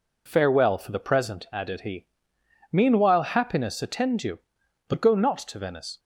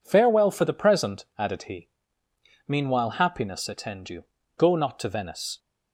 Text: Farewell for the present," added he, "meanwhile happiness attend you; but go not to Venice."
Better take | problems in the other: first | skips "but"; at 4.4 s

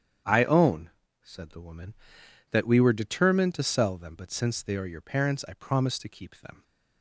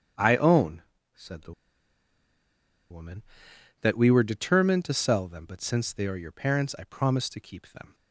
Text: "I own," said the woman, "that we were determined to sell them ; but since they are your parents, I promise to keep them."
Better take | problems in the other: first | starts louder than the rest; strong; until 1.5 s; 8.5 dB; strong in the first // pauses between "the" and "woman"; strong; at 1.5 s; 1.3 s long

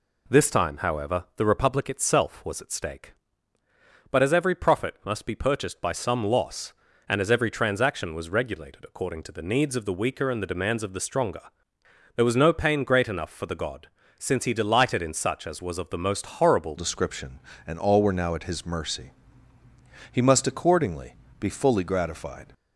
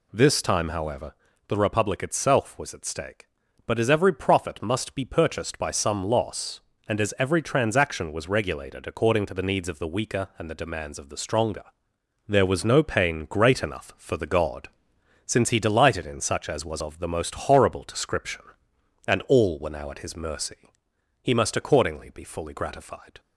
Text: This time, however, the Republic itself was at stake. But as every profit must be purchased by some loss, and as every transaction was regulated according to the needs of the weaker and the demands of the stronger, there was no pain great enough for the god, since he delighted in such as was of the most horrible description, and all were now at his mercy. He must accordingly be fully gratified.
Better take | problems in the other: second | changes voice at "description"; from 16.7 s on; 5.8 s long // pauses between "accordingly" and "be"; slight; at 21.1 s; 0.24 s long

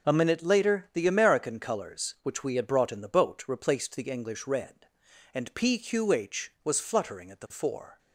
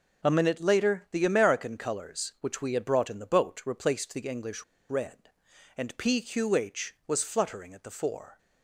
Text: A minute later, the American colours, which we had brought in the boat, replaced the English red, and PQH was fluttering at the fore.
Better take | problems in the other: first | pauses between "English" and "red"; slight; at 4.6 s; 0.25 s long

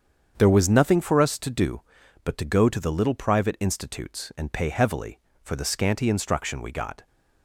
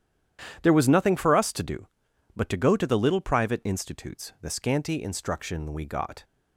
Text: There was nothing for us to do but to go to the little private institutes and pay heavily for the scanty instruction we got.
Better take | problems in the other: first | starts louder than the rest; strong; until 1.6 s; 10 dB; strong in the first // skips "and pay heavily for"; at 4.3 s

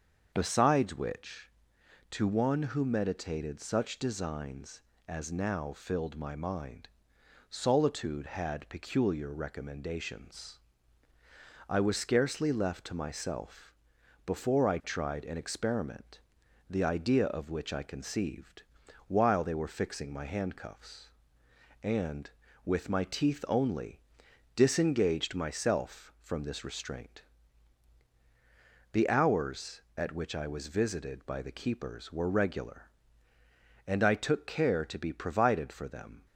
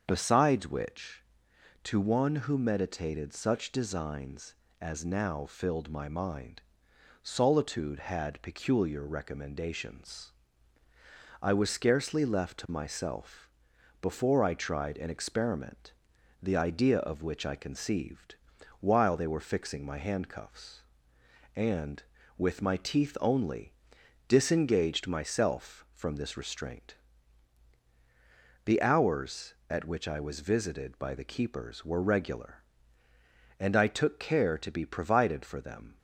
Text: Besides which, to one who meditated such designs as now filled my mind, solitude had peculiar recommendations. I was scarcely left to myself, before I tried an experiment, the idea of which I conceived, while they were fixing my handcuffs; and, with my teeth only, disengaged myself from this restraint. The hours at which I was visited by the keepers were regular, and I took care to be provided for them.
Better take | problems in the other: neither | starts louder than the rest; the same in both

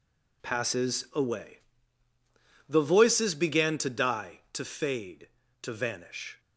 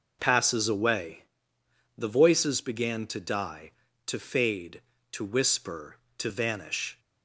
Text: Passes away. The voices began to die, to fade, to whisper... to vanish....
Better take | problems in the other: second | skips "to whisper"; at 5.4 s

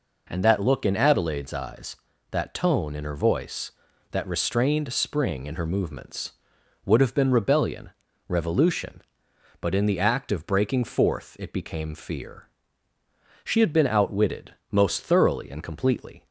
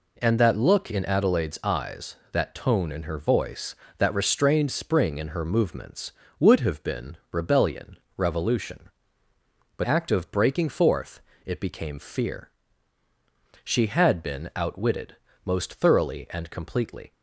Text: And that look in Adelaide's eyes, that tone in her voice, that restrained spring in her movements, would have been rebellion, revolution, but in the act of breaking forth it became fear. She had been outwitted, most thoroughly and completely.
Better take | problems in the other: first | pauses between "been" and "rebellion"; slight; at 7.1 s; 0.16 s long // skips "in the"; at 9.8 s // pauses between "forth" and "it"; slight; at 11.2 s; 0.26 s long

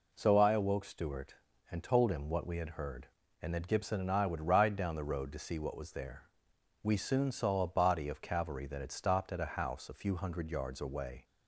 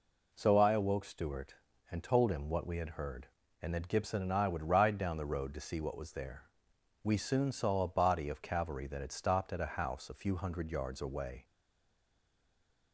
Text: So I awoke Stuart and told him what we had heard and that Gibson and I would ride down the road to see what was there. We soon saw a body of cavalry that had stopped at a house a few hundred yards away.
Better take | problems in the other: first | stays silent after the last word; noticeable; from 11.4 s on; 1.5 s long

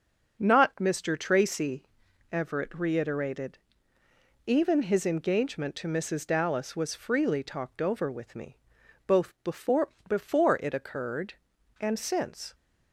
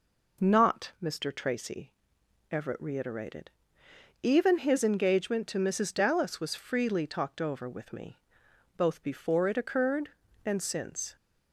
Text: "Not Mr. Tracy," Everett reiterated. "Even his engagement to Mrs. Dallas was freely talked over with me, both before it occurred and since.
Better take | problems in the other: second | says "before" twice; at 10.0 s

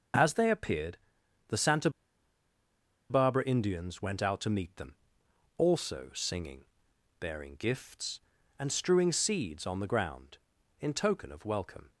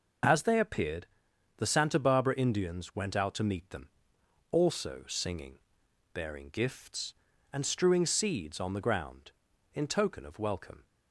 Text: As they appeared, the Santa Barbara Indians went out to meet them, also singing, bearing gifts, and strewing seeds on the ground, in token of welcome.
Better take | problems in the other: second | pauses between "Santa" and "Barbara"; at 1.8 s; 1.2 s long

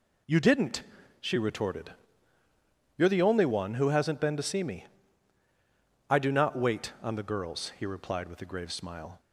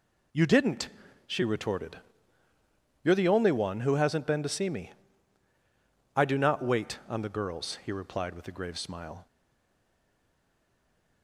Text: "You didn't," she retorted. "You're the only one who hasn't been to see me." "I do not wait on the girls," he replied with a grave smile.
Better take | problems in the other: first | stays silent after the last word; noticeable; from 9.2 s on; 2.0 s long

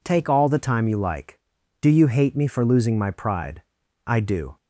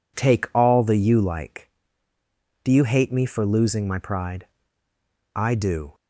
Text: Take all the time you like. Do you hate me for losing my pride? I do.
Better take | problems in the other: first | skips "time"; at 0.9 s

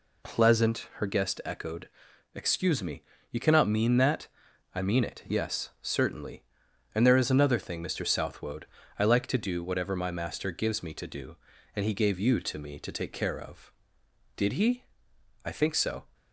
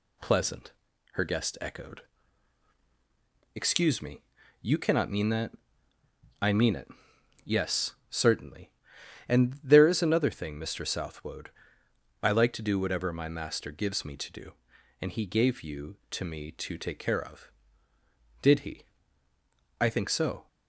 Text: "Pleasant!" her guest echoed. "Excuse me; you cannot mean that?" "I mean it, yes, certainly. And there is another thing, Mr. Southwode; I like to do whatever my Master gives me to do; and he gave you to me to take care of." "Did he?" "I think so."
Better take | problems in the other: neither | none

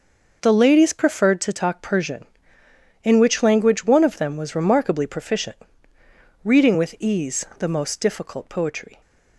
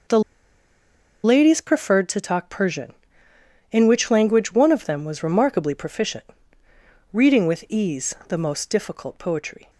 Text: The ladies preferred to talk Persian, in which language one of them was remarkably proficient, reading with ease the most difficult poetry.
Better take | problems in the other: first | pauses between "The" and "ladies"; at 0.2 s; 1.0 s long

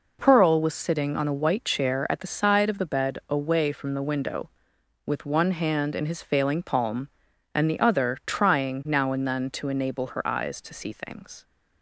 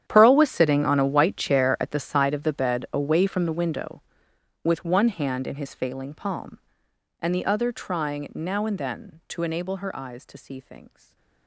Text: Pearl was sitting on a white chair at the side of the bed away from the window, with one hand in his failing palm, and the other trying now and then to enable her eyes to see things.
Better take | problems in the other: first | gets quieter; strong; throughout; 18.5 dB // stays silent after the last word; slight; from 10.8 s on; 0.6 s long

